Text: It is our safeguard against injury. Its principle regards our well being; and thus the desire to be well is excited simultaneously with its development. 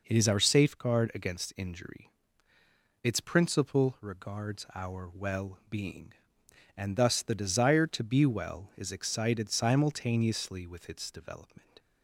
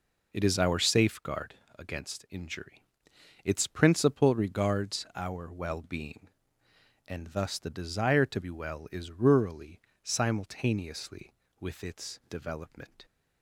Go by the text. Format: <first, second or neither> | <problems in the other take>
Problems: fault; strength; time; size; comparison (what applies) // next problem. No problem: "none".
first | pauses between "safeguard" and "against"; slight; at 1.5 s; 0.24 s long // says "rurally" for "excited"; at 9.0 s